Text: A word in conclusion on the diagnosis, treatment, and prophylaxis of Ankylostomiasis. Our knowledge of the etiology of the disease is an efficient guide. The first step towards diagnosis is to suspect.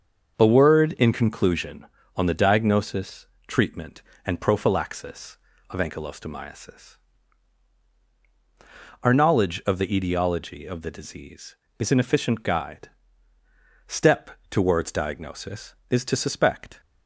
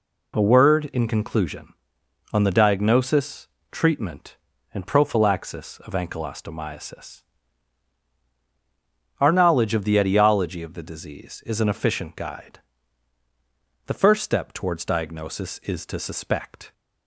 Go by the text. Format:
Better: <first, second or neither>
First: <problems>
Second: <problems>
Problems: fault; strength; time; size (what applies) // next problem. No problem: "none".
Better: second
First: starts louder than the rest; until 1.3 s; 6.5 dB // skips "The first"; at 13.3 s // pauses between "step" and "towards"; slight; at 14.3 s; 0.20 s long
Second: none